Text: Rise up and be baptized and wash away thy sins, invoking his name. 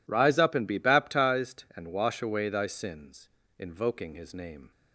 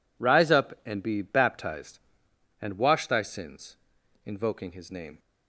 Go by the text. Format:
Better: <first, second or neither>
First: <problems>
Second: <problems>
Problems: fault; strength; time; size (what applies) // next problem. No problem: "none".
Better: first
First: none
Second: skips "away"; at 3.0 s